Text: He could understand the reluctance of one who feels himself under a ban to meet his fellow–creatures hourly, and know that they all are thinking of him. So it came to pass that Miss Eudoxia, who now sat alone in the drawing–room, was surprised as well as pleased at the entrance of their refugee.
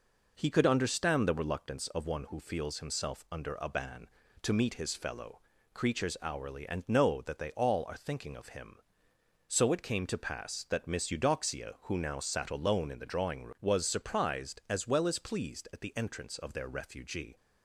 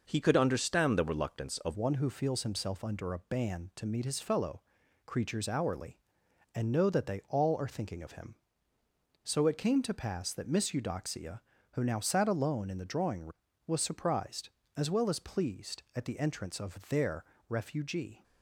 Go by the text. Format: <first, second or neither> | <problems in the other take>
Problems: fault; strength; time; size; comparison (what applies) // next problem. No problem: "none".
first | changes voice at "one"; from 1.7 s on; 16.5 s long // pauses between "their" and "refugee"; slight; at 17.2 s; 0.24 s long